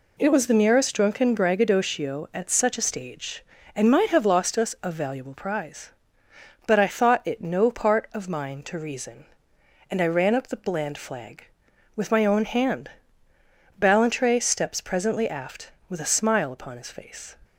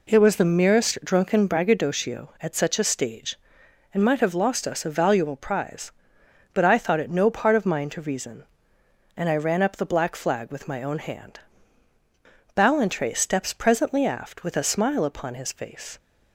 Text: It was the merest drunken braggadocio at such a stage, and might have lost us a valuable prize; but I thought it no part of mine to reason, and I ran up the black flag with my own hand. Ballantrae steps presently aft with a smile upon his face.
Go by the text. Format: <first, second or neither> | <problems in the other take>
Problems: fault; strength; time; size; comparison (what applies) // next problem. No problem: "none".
second | says "bland" for "black"; at 10.5 s